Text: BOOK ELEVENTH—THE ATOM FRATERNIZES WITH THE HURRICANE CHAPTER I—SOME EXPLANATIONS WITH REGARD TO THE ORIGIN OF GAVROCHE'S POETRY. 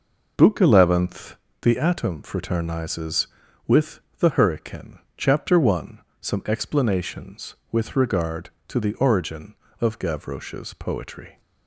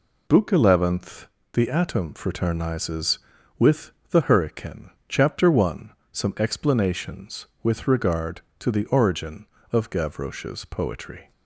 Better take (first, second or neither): second